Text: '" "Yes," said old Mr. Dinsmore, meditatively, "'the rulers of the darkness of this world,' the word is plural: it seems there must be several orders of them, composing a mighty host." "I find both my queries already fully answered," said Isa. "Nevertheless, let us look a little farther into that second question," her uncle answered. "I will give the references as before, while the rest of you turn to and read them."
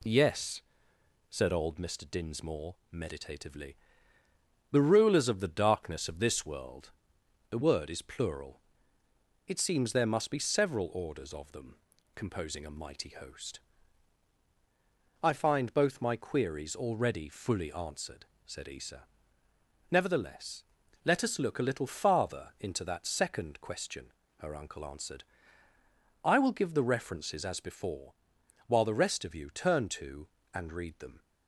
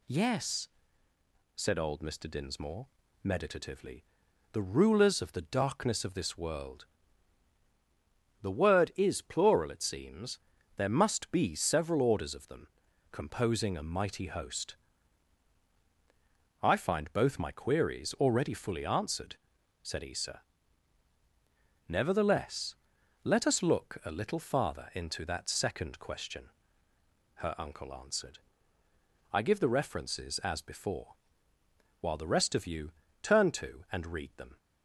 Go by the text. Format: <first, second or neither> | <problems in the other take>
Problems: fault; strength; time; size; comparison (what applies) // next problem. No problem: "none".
first | pauses between "seems" and "there"; slight; at 10.3 s; 0.36 s long // skips "will"; at 29.4 s // pauses between "you" and "turn"; slight; at 32.9 s; 0.30 s long